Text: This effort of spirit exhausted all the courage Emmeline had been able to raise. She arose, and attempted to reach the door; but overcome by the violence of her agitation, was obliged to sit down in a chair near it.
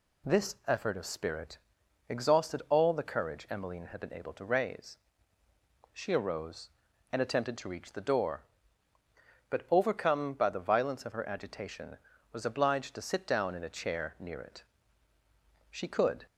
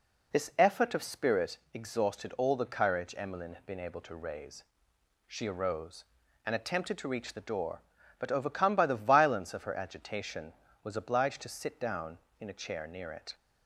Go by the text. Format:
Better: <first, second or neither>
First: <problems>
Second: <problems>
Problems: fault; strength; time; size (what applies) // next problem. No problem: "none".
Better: second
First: pauses between "spirit" and "exhausted"; noticeable; at 1.5 s; 0.50 s long // goes on to say "She could"; from 15.6 s on; 0.56 s long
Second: pauses between "spirit" and "exhausted"; slight; at 1.5 s; 0.16 s long